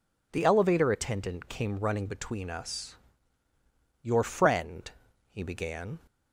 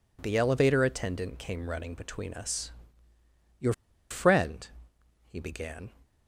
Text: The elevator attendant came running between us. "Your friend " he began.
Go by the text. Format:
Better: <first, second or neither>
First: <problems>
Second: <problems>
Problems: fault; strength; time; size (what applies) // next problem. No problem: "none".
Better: first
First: none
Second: pauses between "Your" and "friend"; at 3.7 s; 0.38 s long